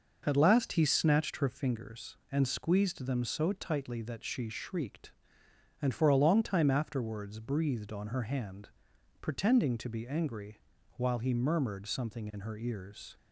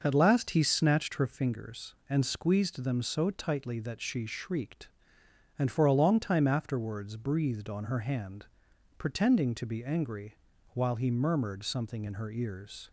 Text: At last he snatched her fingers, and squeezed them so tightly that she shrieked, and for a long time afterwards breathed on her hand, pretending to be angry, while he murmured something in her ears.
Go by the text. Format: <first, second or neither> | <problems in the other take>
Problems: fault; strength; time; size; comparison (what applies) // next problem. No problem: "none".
neither | none